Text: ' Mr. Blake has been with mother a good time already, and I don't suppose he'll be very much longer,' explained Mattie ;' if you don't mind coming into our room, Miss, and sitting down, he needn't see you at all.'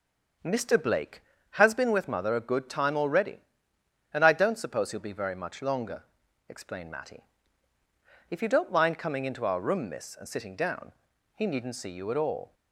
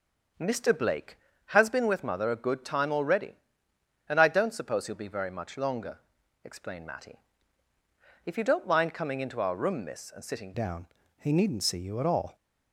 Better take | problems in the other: first | starts louder than the rest; until 1.6 s; 7 dB; also in the first // changes voice at "down"; from 10.5 s on; 1.8 s long

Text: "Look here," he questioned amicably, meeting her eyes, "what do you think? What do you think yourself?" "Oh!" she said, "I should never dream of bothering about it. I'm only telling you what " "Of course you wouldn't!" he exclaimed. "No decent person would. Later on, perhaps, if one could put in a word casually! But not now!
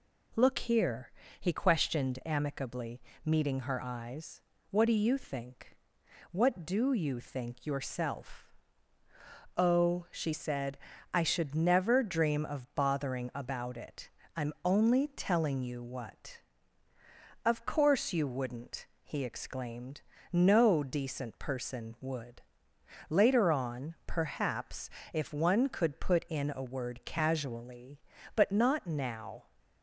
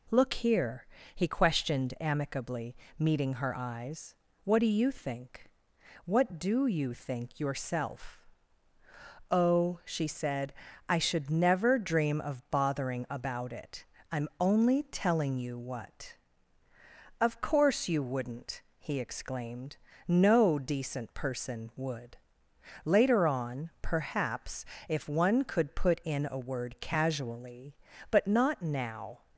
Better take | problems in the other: neither | none

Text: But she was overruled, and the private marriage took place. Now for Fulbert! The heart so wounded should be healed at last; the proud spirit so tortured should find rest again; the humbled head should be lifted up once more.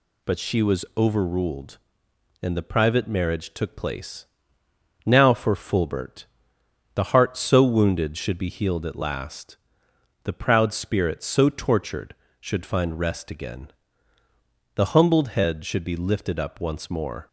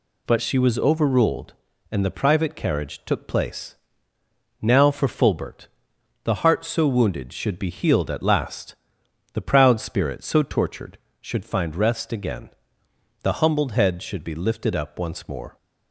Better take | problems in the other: first | says "carriage" for "marriage"; at 2.5 s

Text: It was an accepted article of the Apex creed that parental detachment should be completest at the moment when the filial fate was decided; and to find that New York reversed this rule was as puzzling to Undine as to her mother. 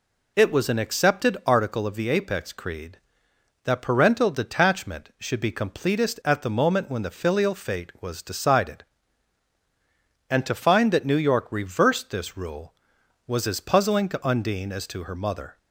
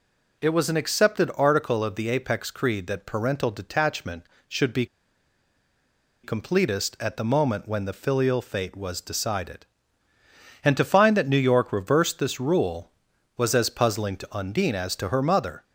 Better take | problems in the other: first | pauses between "be" and "completest"; strong; at 4.8 s; 1.3 s long

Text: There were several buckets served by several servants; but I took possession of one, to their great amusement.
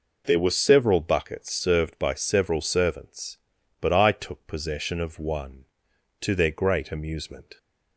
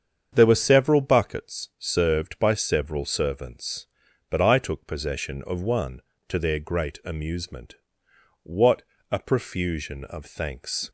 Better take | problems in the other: first | starts louder than the rest; strong; until 1.3 s; 7.5 dB // goes on to say "What a profusion of thanks"; strong; from 8.4 s on; 2.4 s long

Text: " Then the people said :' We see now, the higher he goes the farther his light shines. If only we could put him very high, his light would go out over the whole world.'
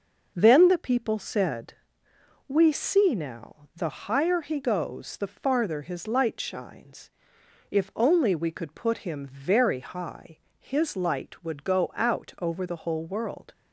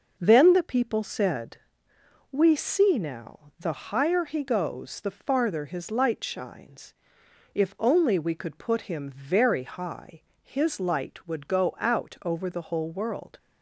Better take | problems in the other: neither | none

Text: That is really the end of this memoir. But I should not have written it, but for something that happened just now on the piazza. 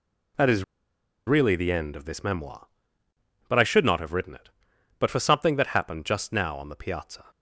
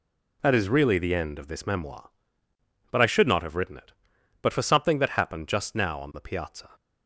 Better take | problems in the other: second | pauses between "is" and "really"; noticeable; at 0.6 s; 0.64 s long

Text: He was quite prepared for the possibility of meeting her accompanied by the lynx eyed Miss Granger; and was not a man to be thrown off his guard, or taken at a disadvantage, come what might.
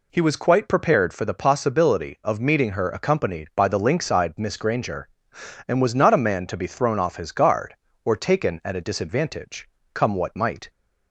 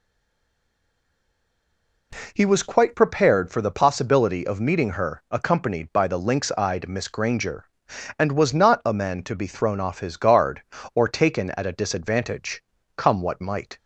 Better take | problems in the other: first | stays silent before the first word; until 2.1 s; 2.1 s long

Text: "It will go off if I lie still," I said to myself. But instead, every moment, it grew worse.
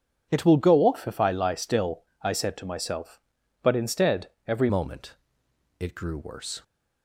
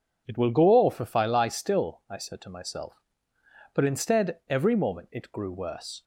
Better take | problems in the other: second | changes voice at "moment"; from 4.6 s on; 2.0 s long

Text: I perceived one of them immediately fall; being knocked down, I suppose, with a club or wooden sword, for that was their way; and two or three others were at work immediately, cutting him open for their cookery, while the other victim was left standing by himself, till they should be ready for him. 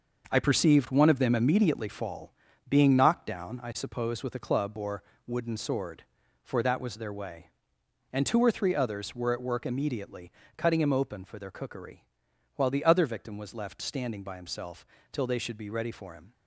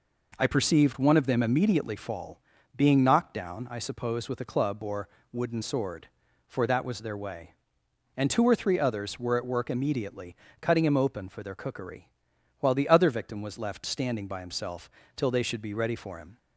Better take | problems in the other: second | gets quieter; strong; throughout; 8.5 dB // pauses between "or" and "wooden"; slight; at 5.0 s; 0.24 s long; slight in the second

